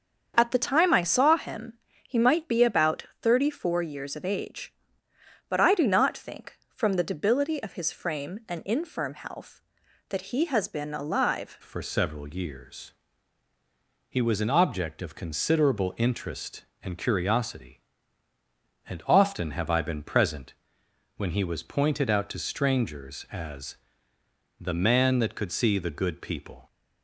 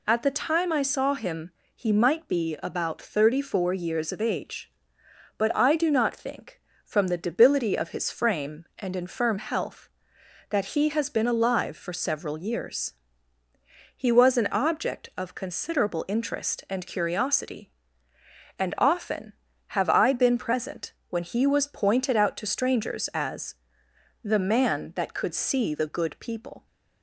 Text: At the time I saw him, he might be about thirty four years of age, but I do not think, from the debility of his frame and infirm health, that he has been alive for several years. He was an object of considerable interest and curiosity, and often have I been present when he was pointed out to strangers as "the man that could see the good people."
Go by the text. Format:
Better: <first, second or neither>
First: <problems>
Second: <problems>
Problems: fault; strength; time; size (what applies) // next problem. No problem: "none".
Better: second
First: starts louder than the rest; strong; until 1.3 s; 7.5 dB // pauses between "about" and "thirty"; slight; at 3.0 s; 0.16 s long // changes voice at "for"; from 11.6 s on; 15.0 s long // pauses between "present" and "when"; noticeable; at 20.5 s; 0.64 s long // pauses between "as" and "the"; noticeable; at 23.7 s; 0.84 s long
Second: pauses between "present" and "when"; slight; at 20.9 s; 0.18 s long // pauses between "as" and "the"; noticeable; at 23.5 s; 0.66 s long